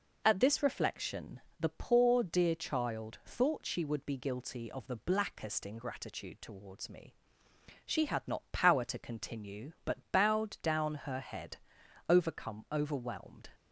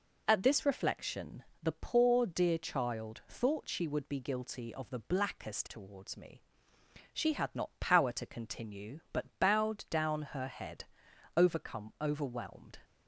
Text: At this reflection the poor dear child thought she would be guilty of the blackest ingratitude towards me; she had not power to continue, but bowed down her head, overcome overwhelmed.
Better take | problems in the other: first | pauses between "reflection" and "the"; slight; at 1.4 s; 0.18 s long; slight in the first // skips "ingratitude"; at 5.6 s

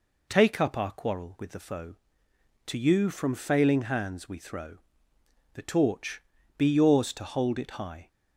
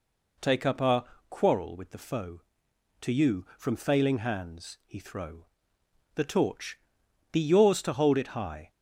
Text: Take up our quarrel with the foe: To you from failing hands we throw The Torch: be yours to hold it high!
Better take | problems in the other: first | pauses between "our" and "quarrel"; slight; at 1.0 s; 0.26 s long // says "he" for "we"; at 4.8 s // pauses between "throw" and "The"; noticeable; at 5.4 s; 0.68 s long; noticeable in the first

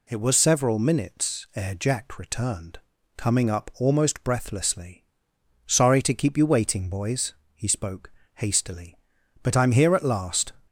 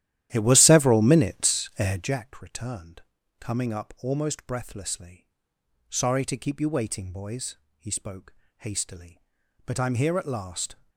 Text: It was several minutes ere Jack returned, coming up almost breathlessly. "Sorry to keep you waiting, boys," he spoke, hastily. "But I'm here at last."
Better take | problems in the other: first | starts louder than the rest; strong; until 2.2 s; 12.5 dB

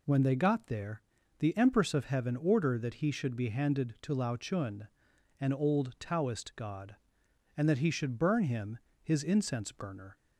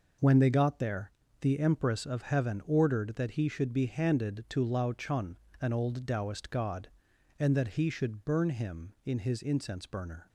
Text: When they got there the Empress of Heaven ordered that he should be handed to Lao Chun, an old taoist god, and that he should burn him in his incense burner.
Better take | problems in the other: second | pauses between "there" and "the"; at 1.0 s; 0.38 s long; slight in the second // skips "in"; at 8.9 s

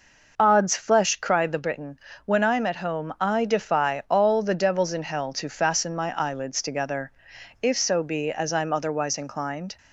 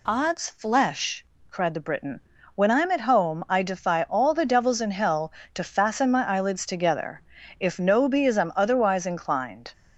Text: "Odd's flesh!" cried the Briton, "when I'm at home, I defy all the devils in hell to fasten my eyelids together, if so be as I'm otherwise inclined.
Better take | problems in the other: first | says "no" for "so"; at 7.8 s

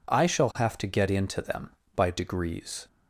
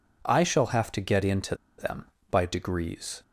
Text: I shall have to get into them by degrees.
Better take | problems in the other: first | pauses between "into" and "them"; slight; at 1.5 s; 0.23 s long

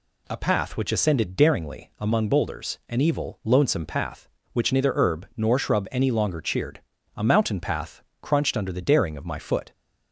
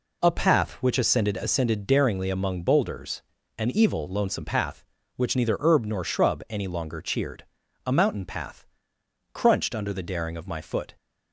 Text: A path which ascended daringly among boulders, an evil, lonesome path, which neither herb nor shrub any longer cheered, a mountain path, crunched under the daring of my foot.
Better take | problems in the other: first | says "ascended" twice; at 1.3 s

